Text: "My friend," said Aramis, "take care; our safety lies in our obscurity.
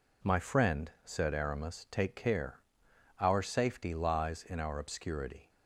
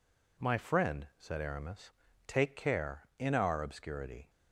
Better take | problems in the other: first | skips "our safety lies"; at 3.1 s

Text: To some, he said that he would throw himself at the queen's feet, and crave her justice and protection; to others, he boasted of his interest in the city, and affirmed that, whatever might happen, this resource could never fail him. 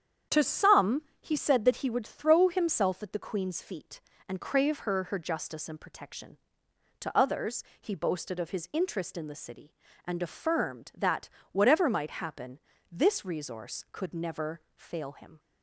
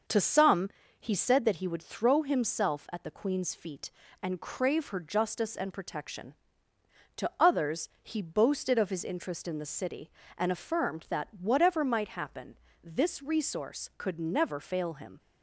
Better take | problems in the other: second | starts louder than the rest; strong; until 1.4 s; 8.5 dB; noticeable in the second // says "her" twice; at 5.0 s // pauses between "never" and "fail"; slight; at 14.5 s; 0.16 s long

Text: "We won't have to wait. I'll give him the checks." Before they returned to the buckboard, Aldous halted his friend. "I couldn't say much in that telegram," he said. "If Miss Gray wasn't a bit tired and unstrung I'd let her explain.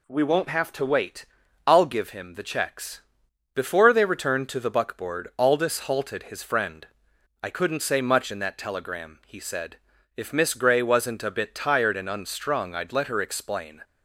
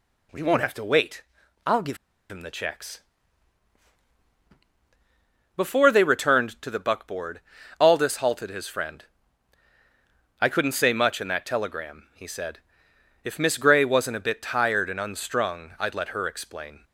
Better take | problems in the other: first | pauses between "give" and "him"; slight; at 1.9 s; 0.32 s long

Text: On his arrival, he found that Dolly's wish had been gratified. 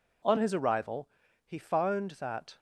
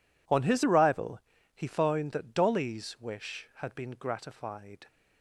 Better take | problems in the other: second | stops before "Dolly's wish had been gratified"; at 2.5 s

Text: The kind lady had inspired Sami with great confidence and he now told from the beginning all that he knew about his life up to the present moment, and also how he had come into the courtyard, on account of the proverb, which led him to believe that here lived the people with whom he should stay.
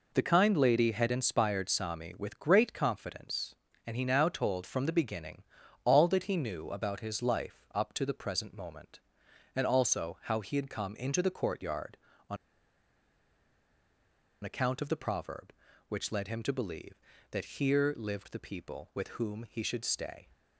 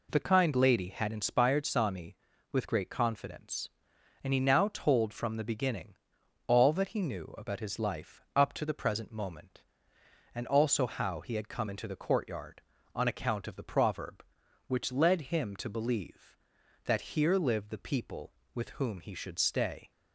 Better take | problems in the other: second | pauses between "beginning" and "all"; at 5.4 s; 0.40 s long; noticeable in the second // pauses between "on" and "account"; strong; at 12.3 s; 2.0 s long

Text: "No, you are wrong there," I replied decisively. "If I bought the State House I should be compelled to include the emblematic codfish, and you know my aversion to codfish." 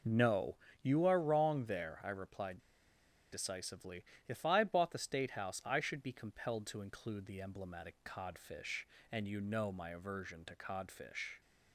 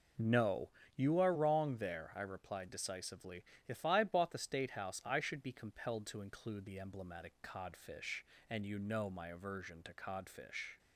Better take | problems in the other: second | pauses between "replied" and "decisively"; noticeable; at 2.5 s; 0.73 s long

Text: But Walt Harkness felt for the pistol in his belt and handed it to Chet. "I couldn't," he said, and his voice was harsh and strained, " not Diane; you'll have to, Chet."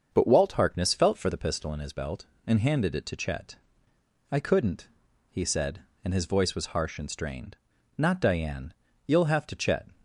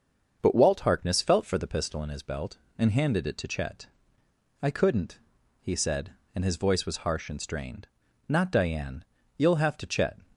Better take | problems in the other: neither | starts louder than the rest; the same in both

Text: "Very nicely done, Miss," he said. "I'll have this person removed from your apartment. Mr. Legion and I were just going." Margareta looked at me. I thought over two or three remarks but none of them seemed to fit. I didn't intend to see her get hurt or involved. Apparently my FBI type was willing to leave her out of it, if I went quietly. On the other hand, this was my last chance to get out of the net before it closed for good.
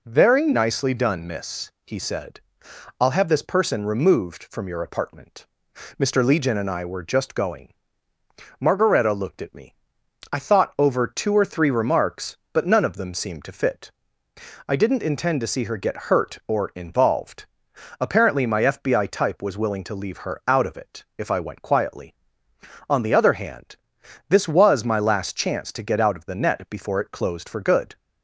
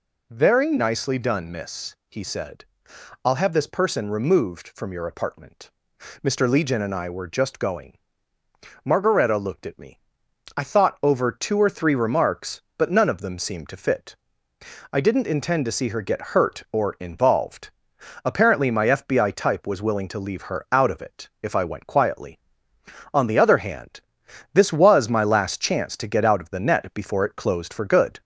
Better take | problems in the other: first | gets louder; slight; throughout; 2 dB

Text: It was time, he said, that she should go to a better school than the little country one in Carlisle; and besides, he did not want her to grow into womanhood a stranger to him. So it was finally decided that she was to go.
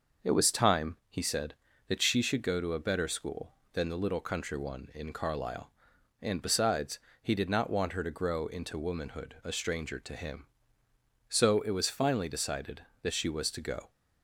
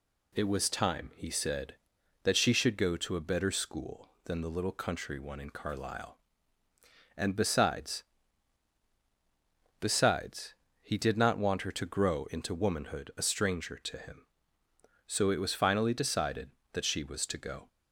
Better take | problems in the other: first | says "besides" twice; at 9.7 s

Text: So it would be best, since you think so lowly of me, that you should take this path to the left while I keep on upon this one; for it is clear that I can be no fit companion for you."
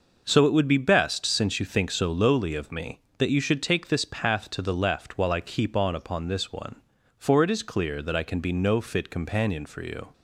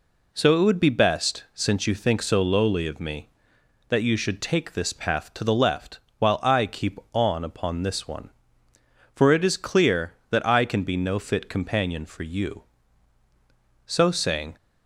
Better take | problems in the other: first | pauses between "left" and "while"; slight; at 5.9 s; 0.20 s long // goes on to say "So saying"; noticeable; from 13.8 s on; 0.70 s long

